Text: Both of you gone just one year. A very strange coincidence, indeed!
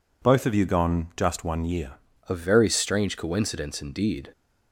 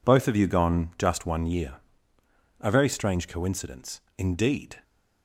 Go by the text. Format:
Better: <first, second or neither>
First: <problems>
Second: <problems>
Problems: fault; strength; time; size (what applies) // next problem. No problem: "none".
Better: second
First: changes voice at "A"; from 2.2 s on; 2.1 s long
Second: none